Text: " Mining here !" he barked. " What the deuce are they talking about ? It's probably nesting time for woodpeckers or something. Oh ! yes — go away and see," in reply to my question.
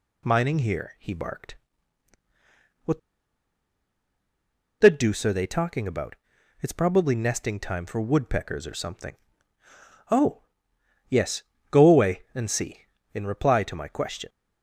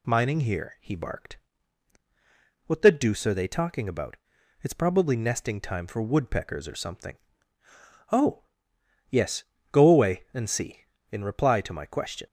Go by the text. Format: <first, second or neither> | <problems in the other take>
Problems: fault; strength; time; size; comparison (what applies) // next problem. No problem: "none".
second | pauses between "What" and "the"; strong; at 2.9 s; 1.8 s long